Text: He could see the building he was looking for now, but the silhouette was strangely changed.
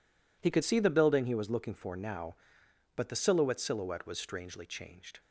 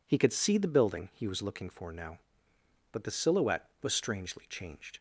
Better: second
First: says "silhouette" twice; at 3.6 s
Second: none

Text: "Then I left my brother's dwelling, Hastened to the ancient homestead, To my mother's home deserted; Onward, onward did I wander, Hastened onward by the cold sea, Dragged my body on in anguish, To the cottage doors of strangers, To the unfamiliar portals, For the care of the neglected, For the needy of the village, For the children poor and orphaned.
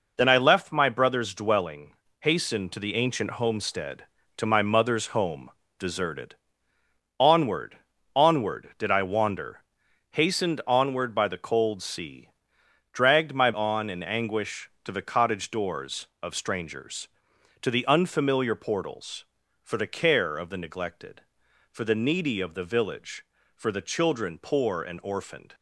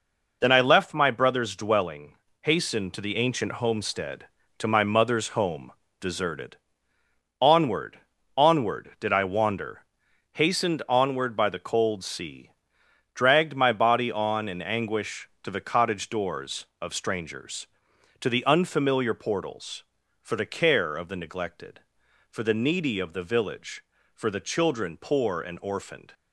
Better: second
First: pauses between "home" and "deserted"; slight; at 5.4 s; 0.28 s long // skips "body"; at 13.5 s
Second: pauses between "home" and "deserted"; slight; at 5.7 s; 0.28 s long

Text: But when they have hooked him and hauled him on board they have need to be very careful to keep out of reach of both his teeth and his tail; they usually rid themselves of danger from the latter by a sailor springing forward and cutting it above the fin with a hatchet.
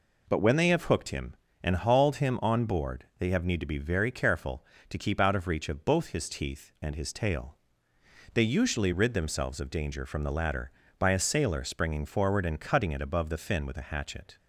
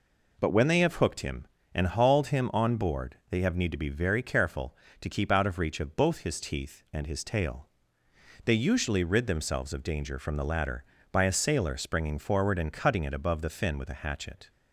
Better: neither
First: none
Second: none

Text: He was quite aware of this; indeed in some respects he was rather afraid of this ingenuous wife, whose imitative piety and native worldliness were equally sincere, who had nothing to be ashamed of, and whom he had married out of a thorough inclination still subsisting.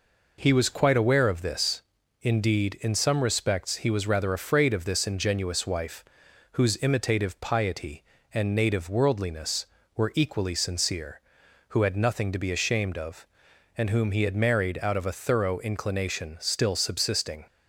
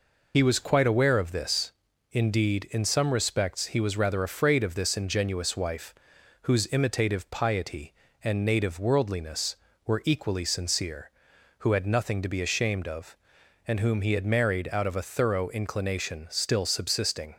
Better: first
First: none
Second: loses the start of "He"; at 0.3 s; 65 ms

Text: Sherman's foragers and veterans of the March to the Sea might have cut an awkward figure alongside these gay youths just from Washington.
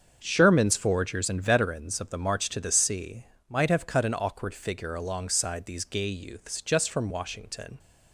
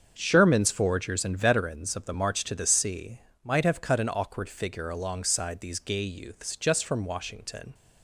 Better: neither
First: starts louder than the rest; until 1.2 s; 7 dB // pauses between "Sea" and "might"; slight; at 3.2 s; 0.24 s long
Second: starts louder than the rest; until 1.1 s; 7 dB // pauses between "Sea" and "might"; slight; at 3.1 s; 0.24 s long

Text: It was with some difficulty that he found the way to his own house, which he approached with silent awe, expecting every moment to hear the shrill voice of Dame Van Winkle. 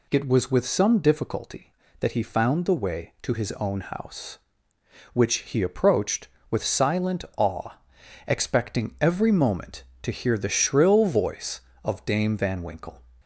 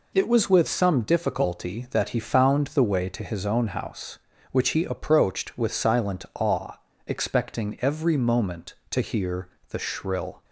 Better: first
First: none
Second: pauses between "hear" and "the"; slight; at 9.4 s; 0.22 s long // stops before "voice of Dame Van Winkle"; at 10.4 s

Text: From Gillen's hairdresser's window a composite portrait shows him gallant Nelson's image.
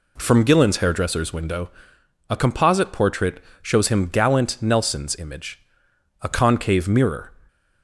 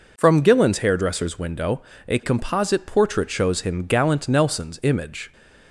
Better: second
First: pauses between "window" and "a"; noticeable; at 1.7 s; 0.58 s long // pauses between "portrait" and "shows"; slight; at 3.4 s; 0.22 s long // goes on to say "A concave mirror"; noticeable; from 6.2 s on; 1.1 s long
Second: pauses between "window" and "a"; slight; at 1.8 s; 0.24 s long

